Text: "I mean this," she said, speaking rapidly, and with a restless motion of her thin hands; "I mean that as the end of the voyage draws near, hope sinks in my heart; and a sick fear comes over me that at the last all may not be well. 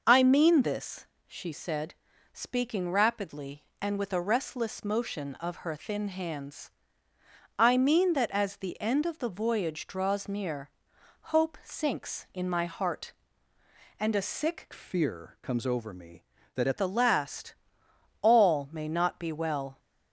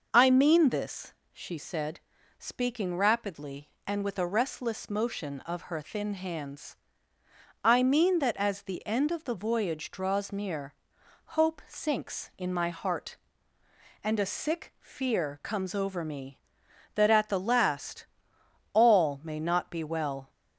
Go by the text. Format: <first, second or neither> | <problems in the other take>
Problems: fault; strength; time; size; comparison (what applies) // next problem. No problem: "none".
second | changes voice from "fear" to "at"; from 14.7 to 16.7 s; 2.0 s long // pauses between "last" and "all"; noticeable; at 17.5 s; 0.66 s long; noticeable in the second